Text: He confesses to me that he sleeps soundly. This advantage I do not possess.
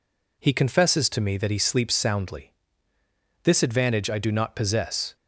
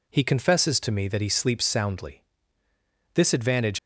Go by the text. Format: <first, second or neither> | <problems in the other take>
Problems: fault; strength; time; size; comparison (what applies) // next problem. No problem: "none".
first | stops before "I do not possess"; at 3.7 s